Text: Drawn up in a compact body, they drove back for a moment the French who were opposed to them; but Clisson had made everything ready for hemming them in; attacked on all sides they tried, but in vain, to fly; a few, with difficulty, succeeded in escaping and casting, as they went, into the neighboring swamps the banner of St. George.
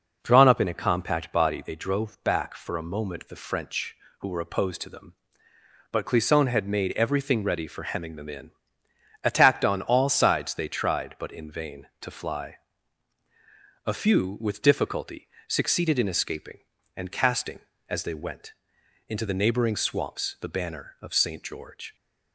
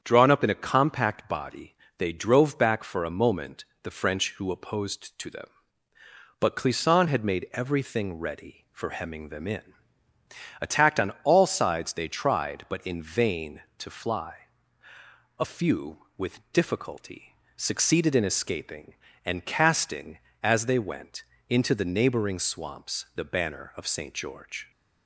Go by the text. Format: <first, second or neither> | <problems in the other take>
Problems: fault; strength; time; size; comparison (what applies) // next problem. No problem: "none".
first | starts louder than the rest; strong; until 1.0 s; 8 dB // pauses between "moment" and "the"; slight; at 3.6 s; 0.18 s long // skips "were"; at 4.5 s